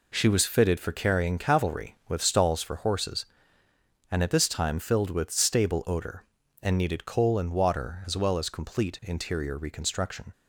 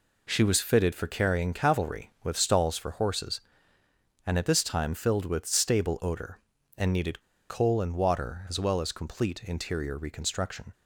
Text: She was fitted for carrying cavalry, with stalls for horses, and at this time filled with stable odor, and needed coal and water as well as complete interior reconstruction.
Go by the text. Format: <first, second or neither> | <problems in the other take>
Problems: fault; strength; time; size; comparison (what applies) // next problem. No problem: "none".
first | pauses between "needed" and "coal"; slight; at 7.2 s; 0.27 s long